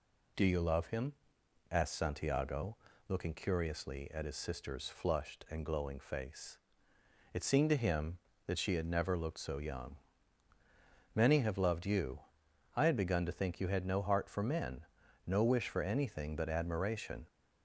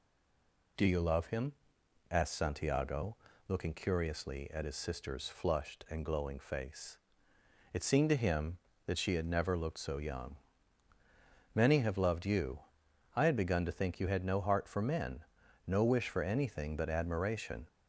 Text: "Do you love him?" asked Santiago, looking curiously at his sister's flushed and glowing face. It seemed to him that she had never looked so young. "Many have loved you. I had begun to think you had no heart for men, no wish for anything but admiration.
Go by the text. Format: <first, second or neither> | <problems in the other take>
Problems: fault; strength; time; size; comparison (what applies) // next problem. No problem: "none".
first | stays silent before the first word; slight; until 0.7 s; 0.7 s long